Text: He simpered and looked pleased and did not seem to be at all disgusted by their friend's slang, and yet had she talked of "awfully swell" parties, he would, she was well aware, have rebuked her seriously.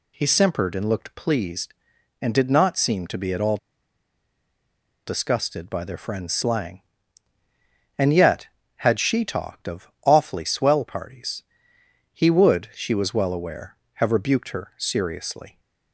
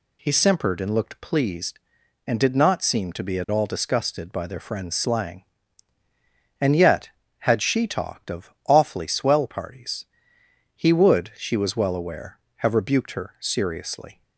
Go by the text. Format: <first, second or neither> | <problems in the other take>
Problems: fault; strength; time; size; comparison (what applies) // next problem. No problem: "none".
second | pauses between "all" and "disgusted"; strong; at 3.5 s; 1.5 s long // pauses between "of" and "awfully"; slight; at 9.8 s; 0.16 s long; slight in the second